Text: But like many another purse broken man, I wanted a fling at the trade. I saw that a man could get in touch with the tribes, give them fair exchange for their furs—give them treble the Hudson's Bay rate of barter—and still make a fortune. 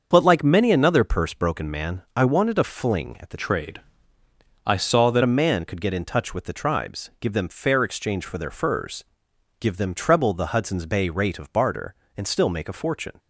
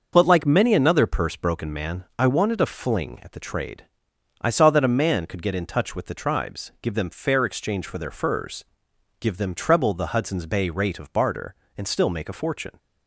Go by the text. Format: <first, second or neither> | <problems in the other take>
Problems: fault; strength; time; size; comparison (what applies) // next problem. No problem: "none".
second | starts louder than the rest; until 1.1 s; 6.5 dB; also in the second // changes voice from "trade" to "that"; from 3.3 to 5.2 s; 1.9 s long